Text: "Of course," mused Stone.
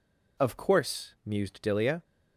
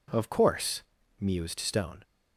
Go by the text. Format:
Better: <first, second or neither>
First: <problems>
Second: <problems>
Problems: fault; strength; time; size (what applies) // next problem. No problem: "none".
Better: second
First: says "Dilia" for "Stone"; at 1.6 s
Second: none